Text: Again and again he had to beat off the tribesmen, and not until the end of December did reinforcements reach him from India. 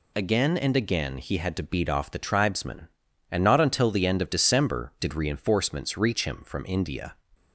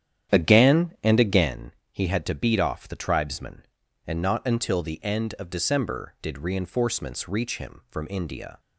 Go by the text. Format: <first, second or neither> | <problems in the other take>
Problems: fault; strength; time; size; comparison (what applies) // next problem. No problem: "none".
first | starts louder than the rest; strong; until 1.5 s; 10 dB // pauses between "again" and "he"; slight; at 1.7 s; 0.22 s long